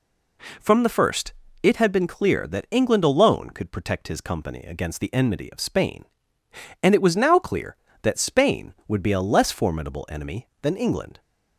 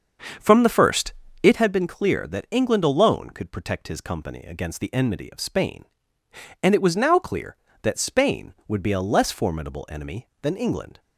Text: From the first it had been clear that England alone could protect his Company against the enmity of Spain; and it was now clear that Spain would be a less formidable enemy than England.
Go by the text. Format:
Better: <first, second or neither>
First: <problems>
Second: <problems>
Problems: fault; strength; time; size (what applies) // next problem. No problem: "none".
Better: first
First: pauses between "first" and "it"; slight; at 1.3 s; 0.30 s long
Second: starts louder than the rest; until 1.7 s; 7 dB // pauses between "first" and "it"; slight; at 1.1 s; 0.30 s long